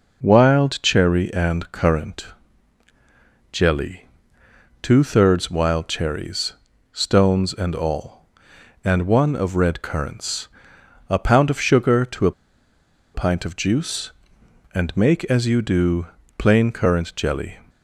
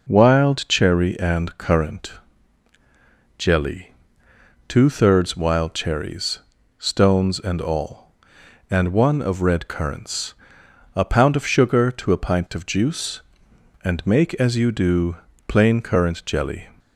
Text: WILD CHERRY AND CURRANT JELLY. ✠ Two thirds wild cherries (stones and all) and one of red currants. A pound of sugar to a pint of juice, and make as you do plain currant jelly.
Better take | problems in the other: second | pauses between "CURRANT" and "JELLY"; at 2.2 s; 1.2 s long; also in the second // pauses between "a" and "pint"; noticeable; at 12.3 s; 0.83 s long // pauses between "do" and "plain"; slight; at 16.0 s; 0.32 s long; slight in the second

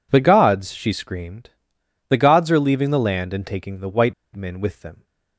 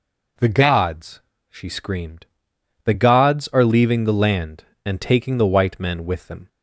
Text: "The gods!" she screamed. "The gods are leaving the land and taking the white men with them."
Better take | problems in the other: second | pauses between "white" and "men"; slight; at 4.1 s; 0.22 s long

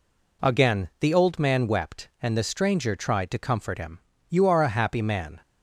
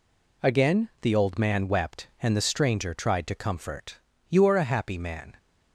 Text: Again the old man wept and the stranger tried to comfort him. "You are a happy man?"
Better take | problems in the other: first | skips "him"; at 4.1 s

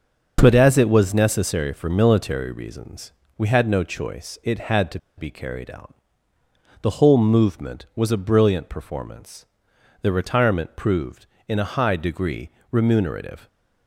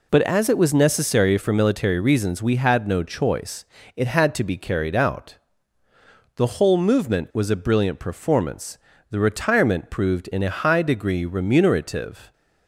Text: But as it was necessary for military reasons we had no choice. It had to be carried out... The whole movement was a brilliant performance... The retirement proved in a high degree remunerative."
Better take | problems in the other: second | starts louder than the rest; until 1.4 s; 6 dB // pauses between "reasons" and "we"; slight; at 3.1 s; 0.26 s long // pauses between "to" and "be"; slight; at 4.9 s; 0.18 s long // pauses between "degree" and "remunerative"; slight; at 12.4 s; 0.22 s long

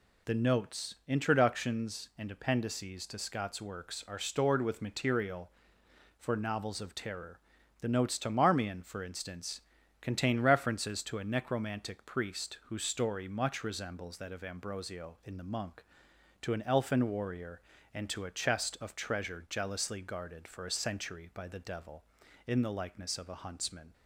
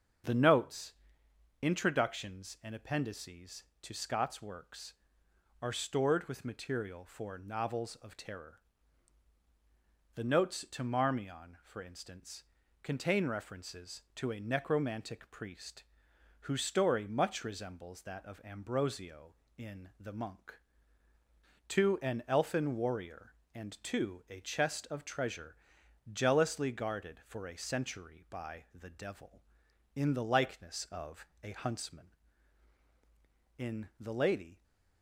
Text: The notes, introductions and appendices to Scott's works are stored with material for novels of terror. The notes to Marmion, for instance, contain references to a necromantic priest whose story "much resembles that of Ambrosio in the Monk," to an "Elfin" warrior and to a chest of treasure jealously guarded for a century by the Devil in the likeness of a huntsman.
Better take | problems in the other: first | starts louder than the rest; until 1.9 s; 7 dB // pauses between "priest" and "whose"; noticeable; at 15.8 s; 0.58 s long // pauses between "treasure" and "jealously"; noticeable; at 25.5 s; 0.52 s long // pauses between "of" and "a"; slight; at 31.2 s; 0.16 s long // goes on to say "In The Lady"; noticeable; from 33.5 s on; 1.0 s long

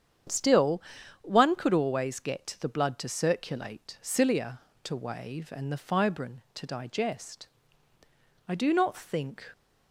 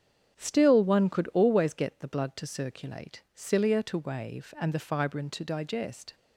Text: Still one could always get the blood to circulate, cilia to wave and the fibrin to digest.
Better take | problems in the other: second | starts louder than the rest; strong; until 1.7 s; 8.5 dB; strong in the second // pauses between "Still" and "one"; at 0.8 s; 0.40 s long // goes on to say "I do not think"; noticeable; from 8.4 s on; 1.0 s long

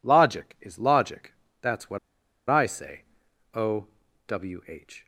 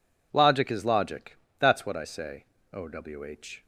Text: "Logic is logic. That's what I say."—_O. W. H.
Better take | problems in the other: second | pauses between "what" and "I"; noticeable; at 1.9 s; 0.51 s long

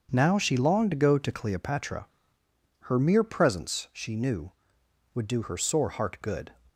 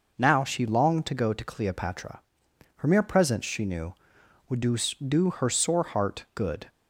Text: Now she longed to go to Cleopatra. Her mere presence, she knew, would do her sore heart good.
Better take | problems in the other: first | says "do" twice; at 5.0 s

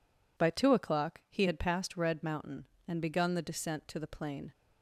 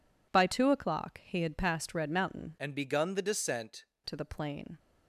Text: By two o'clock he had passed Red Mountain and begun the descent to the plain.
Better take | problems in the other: first | changes voice from "and" to "descent"; from 2.5 to 3.8 s; 1.3 s long

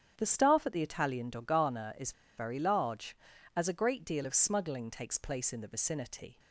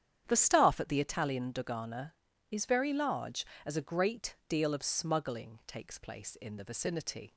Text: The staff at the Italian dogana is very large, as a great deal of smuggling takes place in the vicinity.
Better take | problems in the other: second | starts louder than the rest; strong; until 1.1 s; 9.5 dB; strong in the second // pauses between "is" and "very"; slight; at 2.1 s; 0.25 s long

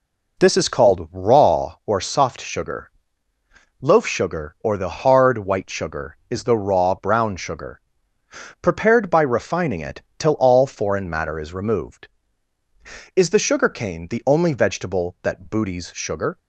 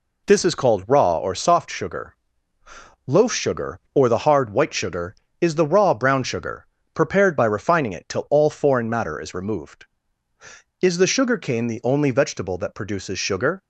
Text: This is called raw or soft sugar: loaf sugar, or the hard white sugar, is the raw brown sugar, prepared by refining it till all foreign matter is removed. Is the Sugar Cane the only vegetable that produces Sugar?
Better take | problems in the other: second | pauses between "it" and "till"; slight; at 10.0 s; 0.18 s long // says "booties" for "produces"; at 15.4 s

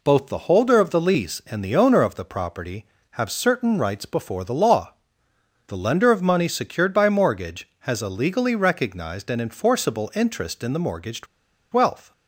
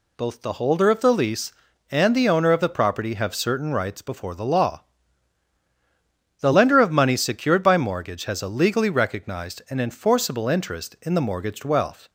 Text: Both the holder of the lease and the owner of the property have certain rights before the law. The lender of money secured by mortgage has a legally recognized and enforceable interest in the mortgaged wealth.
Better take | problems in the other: second | pauses between "mortgaged" and "wealth"; noticeable; at 11.2 s; 0.47 s long

